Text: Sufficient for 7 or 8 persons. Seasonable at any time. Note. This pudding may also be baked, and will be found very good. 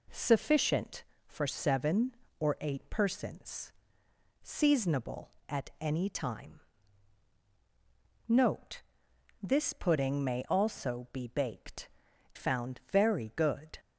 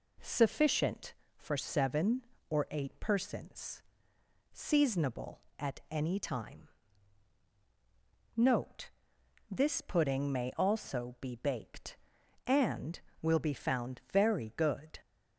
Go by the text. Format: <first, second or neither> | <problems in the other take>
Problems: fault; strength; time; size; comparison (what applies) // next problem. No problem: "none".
second | skips "and will be"; at 12.1 s